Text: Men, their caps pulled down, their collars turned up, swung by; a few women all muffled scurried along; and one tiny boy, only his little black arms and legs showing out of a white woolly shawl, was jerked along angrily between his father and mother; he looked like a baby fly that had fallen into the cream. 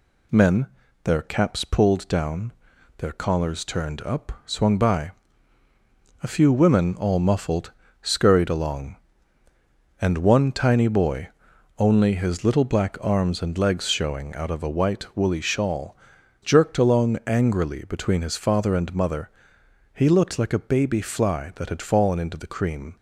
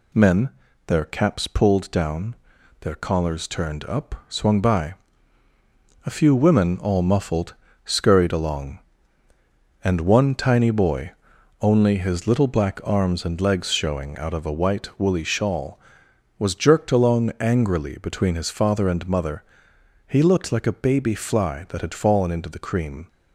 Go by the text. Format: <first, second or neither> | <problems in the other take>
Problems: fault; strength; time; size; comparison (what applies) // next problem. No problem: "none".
second | pauses between "muffled" and "scurried"; slight; at 7.7 s; 0.28 s long; slight in the second // skips "was"; at 16.1 s